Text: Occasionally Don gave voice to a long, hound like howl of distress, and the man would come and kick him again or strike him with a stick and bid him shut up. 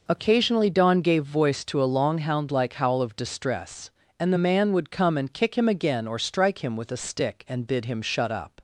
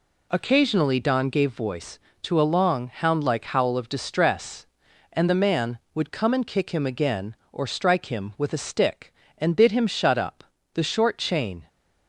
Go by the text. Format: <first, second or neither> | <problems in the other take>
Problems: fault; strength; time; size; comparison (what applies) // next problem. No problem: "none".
first | goes on to say "The short chain"; noticeable; from 10.7 s on; 0.94 s long